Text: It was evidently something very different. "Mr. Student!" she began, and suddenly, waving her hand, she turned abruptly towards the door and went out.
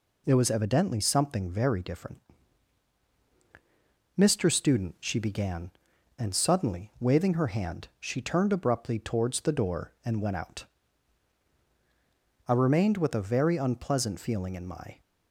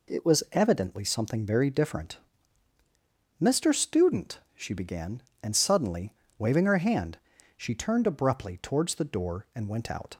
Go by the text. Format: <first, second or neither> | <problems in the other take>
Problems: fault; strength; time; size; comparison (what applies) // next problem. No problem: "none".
second | goes on to say "I remained with a very unpleasant feeling in my"; strong; from 12.4 s on; 2.5 s long